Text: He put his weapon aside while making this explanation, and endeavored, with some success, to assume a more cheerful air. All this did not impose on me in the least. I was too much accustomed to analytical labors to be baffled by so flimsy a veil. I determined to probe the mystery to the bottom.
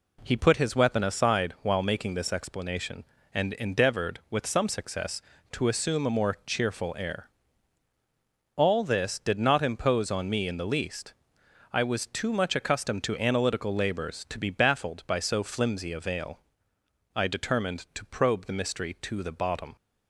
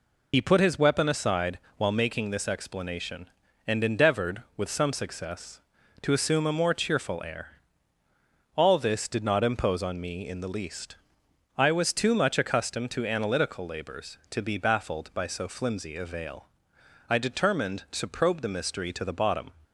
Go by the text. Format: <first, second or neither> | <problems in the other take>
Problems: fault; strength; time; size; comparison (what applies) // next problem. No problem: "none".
first | loses the start of "He"; at 0.3 s; 55 ms // pauses between "aside" and "while"; slight; at 1.5 s; 0.20 s long